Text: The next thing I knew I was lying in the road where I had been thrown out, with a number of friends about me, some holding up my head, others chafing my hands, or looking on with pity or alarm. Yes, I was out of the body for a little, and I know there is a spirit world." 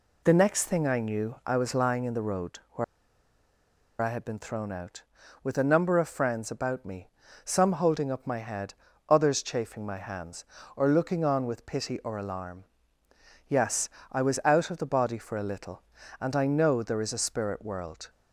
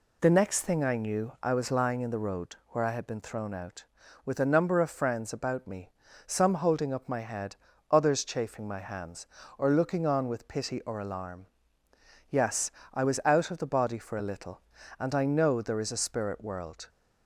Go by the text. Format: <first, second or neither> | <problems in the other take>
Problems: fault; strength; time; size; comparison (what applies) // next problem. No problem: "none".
second | pauses between "where" and "I"; at 2.8 s; 1.1 s long